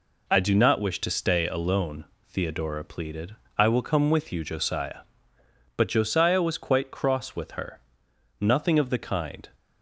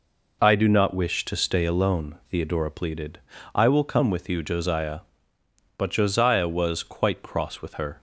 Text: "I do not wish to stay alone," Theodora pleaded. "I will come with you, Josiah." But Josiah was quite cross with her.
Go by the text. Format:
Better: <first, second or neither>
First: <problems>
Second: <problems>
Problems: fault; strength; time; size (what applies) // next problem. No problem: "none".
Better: second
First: goes on to say "Nothing of the kind"; noticeable; from 8.4 s on; 1.0 s long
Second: none